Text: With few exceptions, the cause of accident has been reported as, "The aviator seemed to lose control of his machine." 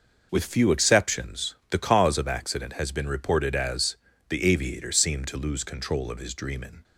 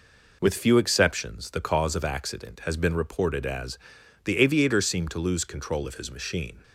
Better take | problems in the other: second | says "dreamin" for "machine"; at 6.3 s

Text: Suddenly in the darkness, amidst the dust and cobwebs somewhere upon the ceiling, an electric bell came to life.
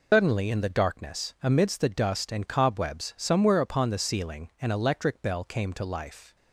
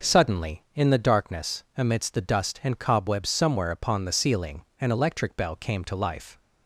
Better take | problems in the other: second | loses the start of "Suddenly"; at 0.1 s; 160 ms

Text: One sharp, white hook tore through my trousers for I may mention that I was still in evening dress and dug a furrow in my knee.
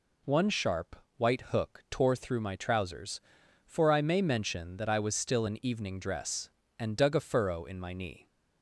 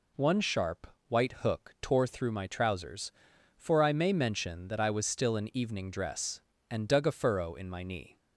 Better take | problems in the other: neither | none

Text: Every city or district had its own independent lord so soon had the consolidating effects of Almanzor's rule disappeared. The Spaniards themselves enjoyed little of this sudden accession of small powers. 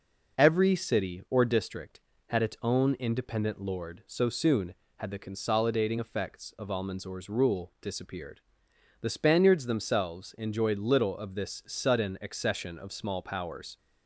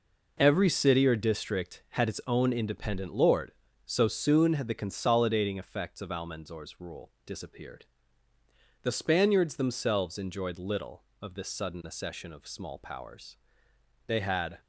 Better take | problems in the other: first | goes on to say "They had"; from 14.0 s on; 0.54 s long

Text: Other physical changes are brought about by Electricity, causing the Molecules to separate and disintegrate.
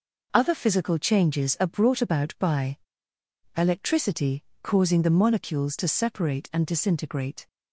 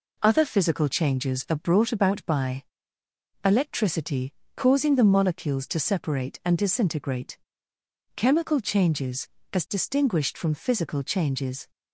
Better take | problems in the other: first | pauses between "by" and "Electricity"; noticeable; at 2.6 s; 0.82 s long; noticeable in the first // goes on to say "Chemical Changes as distinguished from Physical Changes"; strong; from 8.1 s on; 3.5 s long

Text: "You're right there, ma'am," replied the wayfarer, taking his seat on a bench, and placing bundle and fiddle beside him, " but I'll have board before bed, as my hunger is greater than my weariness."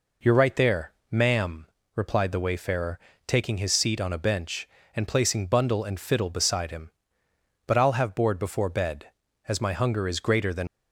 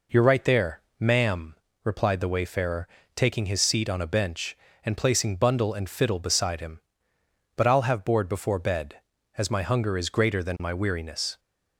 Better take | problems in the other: second | stops before "my weariness"; at 10.6 s

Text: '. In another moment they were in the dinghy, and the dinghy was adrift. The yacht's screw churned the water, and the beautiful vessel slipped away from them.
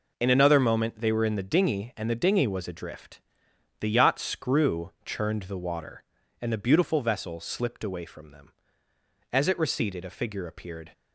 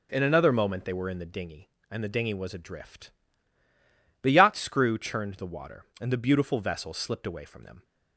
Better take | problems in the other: second | goes on to say "As it receded a figure appeared"; from 9.3 s on; 1.6 s long

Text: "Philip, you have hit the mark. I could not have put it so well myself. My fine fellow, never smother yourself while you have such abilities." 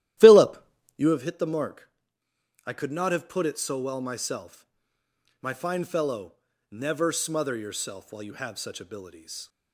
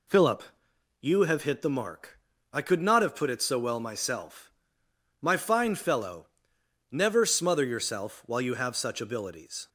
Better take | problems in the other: second | starts louder than the rest; strong; until 1.2 s; 13.5 dB

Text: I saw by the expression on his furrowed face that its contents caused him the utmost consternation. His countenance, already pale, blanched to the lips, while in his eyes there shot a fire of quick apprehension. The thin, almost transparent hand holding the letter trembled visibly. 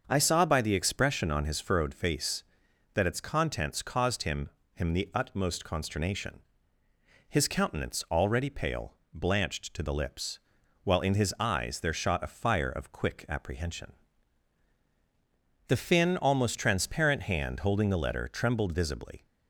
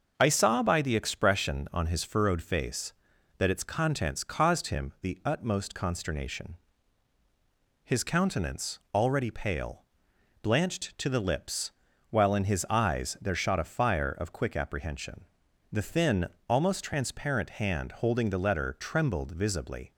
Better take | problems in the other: second | starts louder than the rest; until 1.0 s; 6.5 dB; noticeable in the second // says "him" twice; at 4.7 s

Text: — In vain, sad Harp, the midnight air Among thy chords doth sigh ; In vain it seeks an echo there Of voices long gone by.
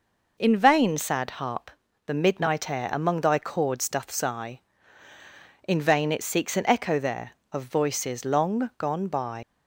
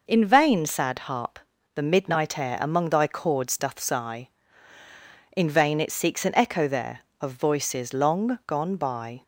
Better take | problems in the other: second | leaves "by" unfinished; at 9.4 s; 110 ms

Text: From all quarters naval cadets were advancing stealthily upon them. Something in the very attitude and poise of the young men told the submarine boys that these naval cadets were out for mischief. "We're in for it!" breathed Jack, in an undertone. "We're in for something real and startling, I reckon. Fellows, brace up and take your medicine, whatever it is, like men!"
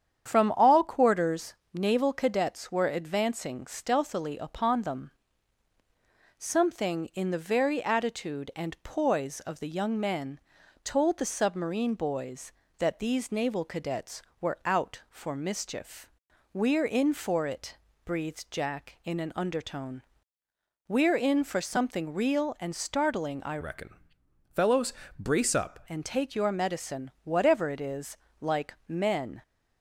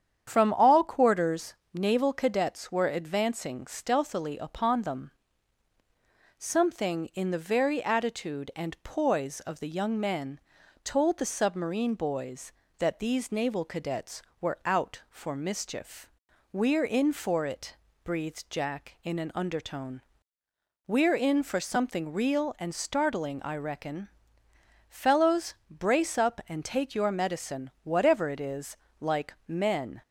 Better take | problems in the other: second | starts louder than the rest; strong; until 1.3 s; 8.5 dB; strong in the second // pauses between "quarters" and "naval"; slight; at 1.5 s; 0.18 s long; slight in the second // pauses between "men" and "told"; at 10.4 s; 0.42 s long; also in the second // changes voice from "reckon" to "up"; from 23.6 to 25.8 s; 2.2 s long

